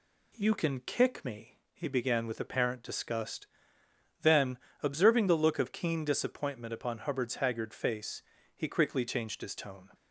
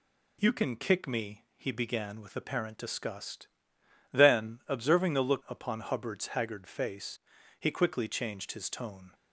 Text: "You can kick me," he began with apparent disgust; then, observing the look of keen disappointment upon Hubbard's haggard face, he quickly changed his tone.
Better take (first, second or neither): first